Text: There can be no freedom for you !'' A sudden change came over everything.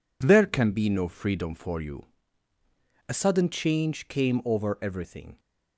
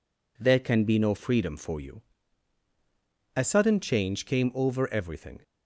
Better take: neither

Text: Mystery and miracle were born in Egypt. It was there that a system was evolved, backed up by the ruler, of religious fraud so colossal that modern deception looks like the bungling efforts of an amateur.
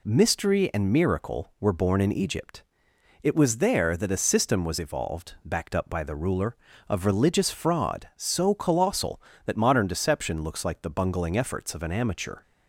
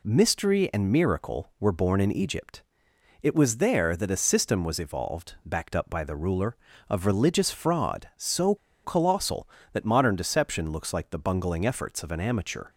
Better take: first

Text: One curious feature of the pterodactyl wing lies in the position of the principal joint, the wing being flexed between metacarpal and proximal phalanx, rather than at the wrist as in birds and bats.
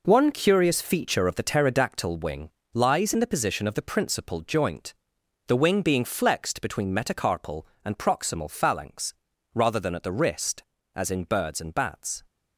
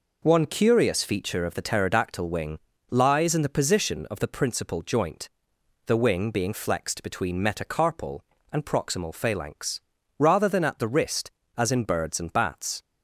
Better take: second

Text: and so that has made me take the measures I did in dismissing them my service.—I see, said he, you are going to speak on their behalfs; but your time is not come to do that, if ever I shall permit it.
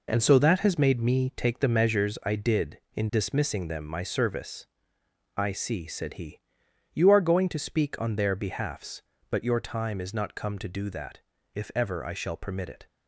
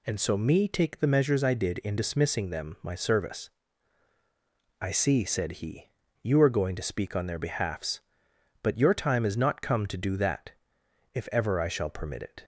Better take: first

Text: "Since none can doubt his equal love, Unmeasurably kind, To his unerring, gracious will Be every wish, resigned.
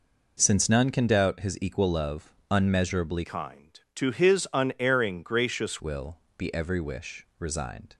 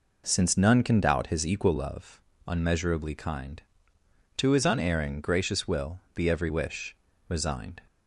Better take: second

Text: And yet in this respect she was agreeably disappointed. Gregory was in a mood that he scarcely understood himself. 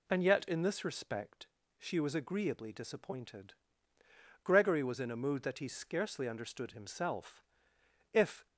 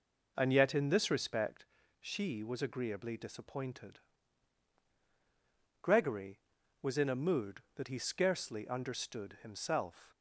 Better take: second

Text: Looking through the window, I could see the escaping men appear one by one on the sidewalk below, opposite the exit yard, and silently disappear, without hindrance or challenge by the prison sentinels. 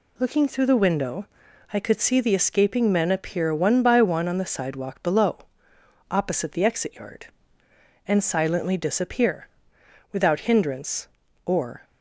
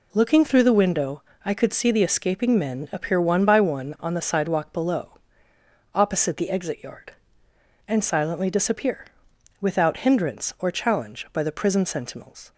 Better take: second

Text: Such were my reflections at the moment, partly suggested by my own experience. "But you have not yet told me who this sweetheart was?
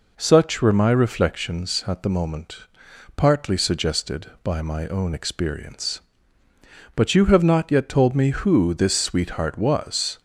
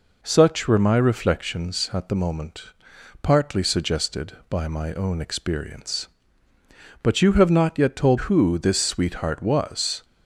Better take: first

